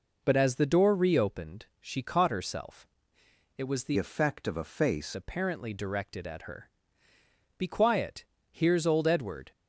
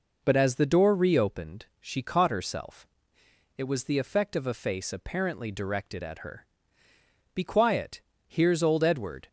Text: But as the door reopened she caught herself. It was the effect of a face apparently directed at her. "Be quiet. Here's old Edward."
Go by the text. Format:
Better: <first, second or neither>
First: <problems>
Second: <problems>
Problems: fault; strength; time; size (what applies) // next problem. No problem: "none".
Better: second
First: changes voice from "effect" to "face"; from 3.9 to 5.1 s; 1.2 s long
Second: none